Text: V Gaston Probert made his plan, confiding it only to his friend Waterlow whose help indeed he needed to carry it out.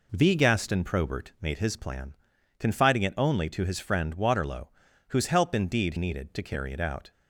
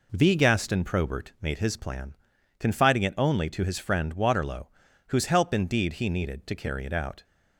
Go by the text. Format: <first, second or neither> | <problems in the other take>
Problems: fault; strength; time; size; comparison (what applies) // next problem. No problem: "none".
second | pauses between "Waterlow" and "whose"; at 4.6 s; 0.40 s long; also in the second // skips "he"; at 5.9 s